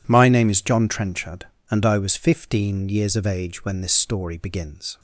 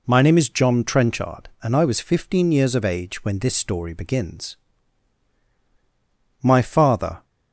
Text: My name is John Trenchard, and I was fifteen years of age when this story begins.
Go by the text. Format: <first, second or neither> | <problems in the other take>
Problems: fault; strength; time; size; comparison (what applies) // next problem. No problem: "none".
first | goes on to say "My father"; noticeable; from 6.4 s on; 0.82 s long